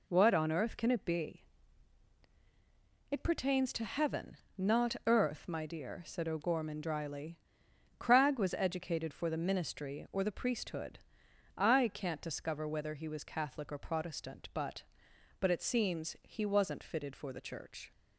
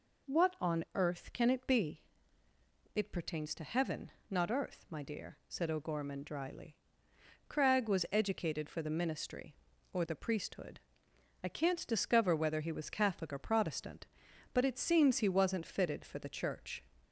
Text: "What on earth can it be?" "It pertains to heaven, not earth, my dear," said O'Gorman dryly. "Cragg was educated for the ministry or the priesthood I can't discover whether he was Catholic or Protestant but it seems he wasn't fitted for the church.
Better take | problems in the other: second | pauses between "priesthood" and "I"; noticeable; at 10.9 s; 0.58 s long; noticeable in the second // says "but" twice; at 15.3 s

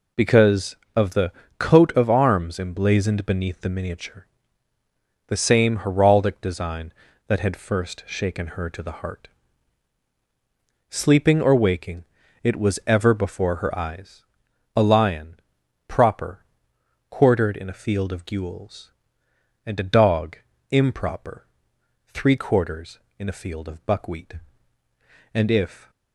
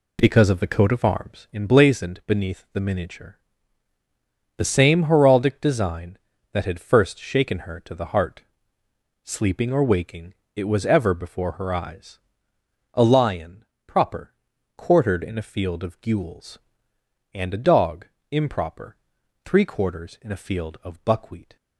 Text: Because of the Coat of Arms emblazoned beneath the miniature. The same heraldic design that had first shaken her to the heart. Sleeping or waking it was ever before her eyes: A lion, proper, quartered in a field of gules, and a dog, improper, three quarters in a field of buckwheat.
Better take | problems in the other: second | pauses between "the" and "Coat"; slight; at 1.3 s; 0.26 s long // pauses between "waking" and "it"; at 12.0 s; 0.38 s long; slight in the second // goes on to say "And if"; from 25.3 s on; 0.58 s long

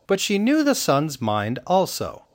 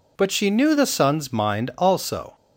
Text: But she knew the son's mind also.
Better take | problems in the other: neither | none

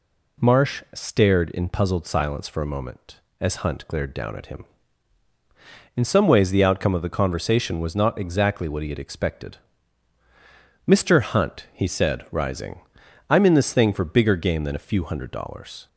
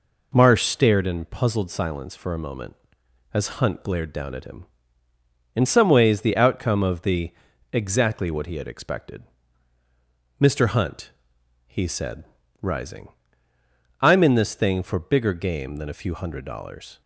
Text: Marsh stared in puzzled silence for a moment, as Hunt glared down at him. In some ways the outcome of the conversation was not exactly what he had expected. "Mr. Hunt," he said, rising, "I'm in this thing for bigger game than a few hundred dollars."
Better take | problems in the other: first | skips "conversation was not"; at 7.5 s

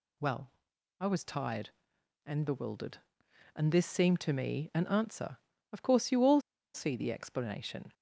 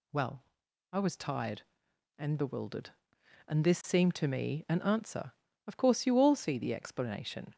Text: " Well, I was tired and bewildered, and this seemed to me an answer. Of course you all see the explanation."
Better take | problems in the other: second | pauses between "all" and "see"; slight; at 6.4 s; 0.33 s long

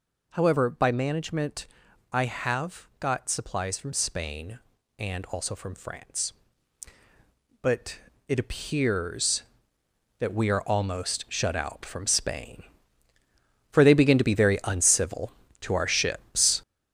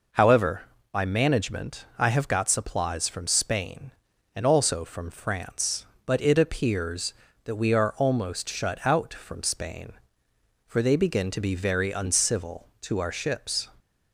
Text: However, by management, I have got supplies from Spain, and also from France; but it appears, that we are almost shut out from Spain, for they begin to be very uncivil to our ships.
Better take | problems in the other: second | gets louder; noticeable; throughout; 5.5 dB // pauses between "but" and "it"; slight; at 7.9 s; 0.30 s long

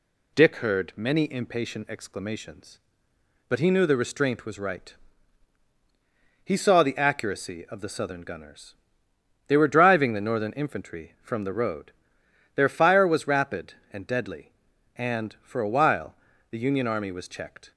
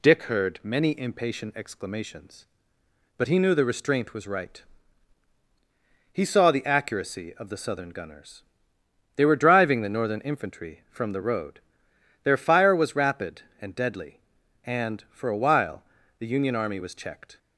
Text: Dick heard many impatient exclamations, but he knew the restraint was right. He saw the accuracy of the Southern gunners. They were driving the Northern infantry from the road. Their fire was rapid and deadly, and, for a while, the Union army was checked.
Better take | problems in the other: neither | none

